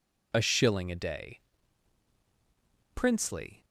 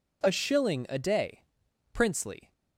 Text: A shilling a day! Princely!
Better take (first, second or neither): neither